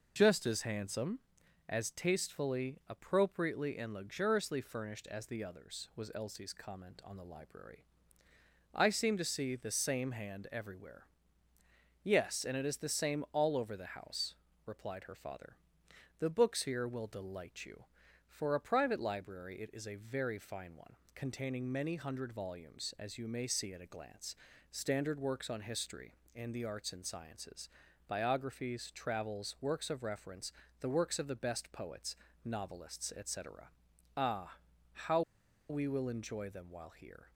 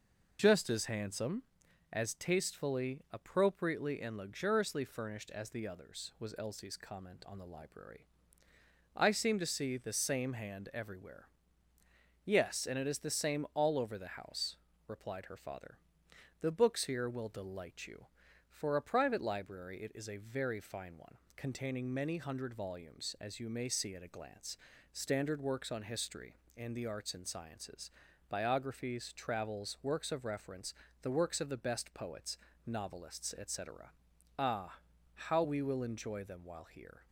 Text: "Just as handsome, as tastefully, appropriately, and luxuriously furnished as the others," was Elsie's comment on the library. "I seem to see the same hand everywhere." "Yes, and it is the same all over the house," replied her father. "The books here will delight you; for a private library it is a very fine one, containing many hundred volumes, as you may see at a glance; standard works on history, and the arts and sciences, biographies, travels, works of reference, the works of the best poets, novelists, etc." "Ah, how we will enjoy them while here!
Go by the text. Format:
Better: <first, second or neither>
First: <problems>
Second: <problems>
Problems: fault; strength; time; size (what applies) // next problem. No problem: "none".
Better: second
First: pauses between "how" and "we"; noticeable; at 35.2 s; 0.48 s long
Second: none